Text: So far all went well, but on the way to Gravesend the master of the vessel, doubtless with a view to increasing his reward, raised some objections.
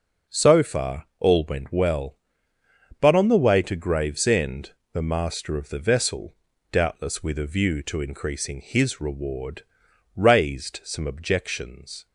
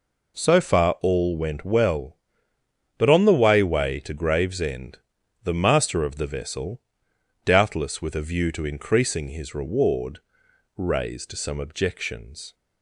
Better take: first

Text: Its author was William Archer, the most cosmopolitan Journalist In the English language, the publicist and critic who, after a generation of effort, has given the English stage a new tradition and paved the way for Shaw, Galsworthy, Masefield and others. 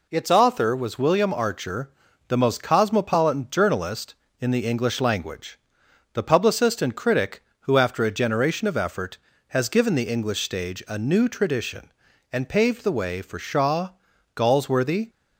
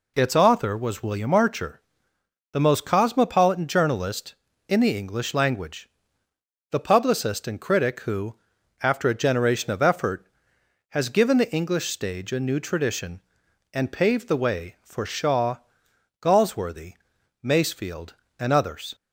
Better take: second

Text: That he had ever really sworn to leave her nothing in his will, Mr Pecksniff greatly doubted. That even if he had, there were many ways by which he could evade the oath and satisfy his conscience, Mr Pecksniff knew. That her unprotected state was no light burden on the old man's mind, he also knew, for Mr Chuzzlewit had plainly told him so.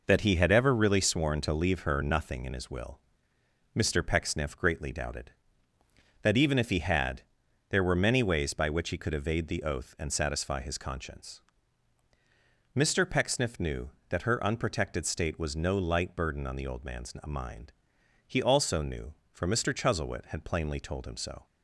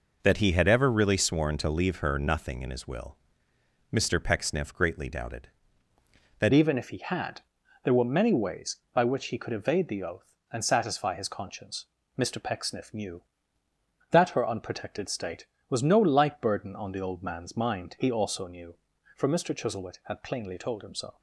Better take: first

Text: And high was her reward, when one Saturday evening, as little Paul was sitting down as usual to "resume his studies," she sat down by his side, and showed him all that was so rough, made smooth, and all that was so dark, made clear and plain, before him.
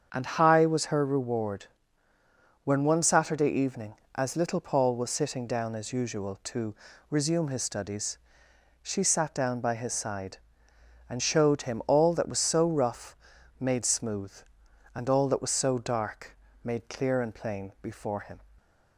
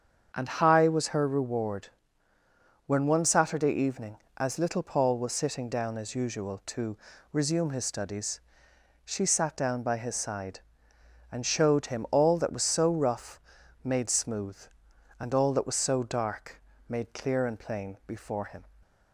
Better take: neither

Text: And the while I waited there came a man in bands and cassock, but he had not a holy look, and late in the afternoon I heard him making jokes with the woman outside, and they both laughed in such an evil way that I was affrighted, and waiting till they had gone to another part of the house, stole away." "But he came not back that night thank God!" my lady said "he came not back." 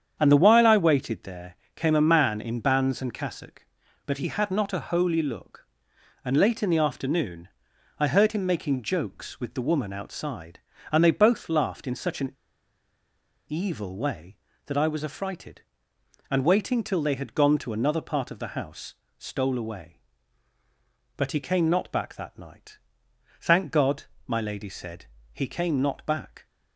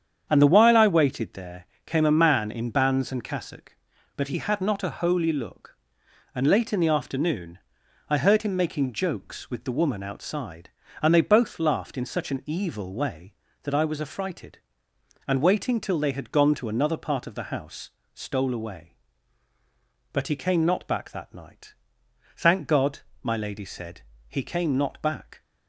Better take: second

